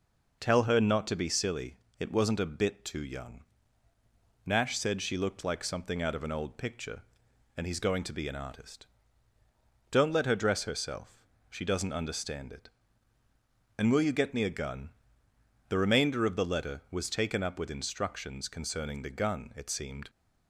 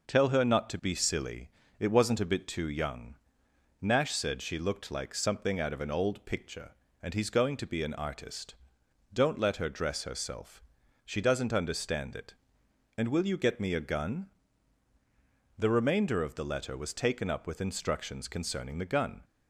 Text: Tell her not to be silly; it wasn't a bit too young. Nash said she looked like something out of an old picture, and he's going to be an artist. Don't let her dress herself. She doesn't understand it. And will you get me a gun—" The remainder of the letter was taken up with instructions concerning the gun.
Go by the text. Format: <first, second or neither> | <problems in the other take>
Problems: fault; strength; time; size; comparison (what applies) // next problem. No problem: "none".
second | goes on to say "It seemed"; from 19.5 s on; 0.54 s long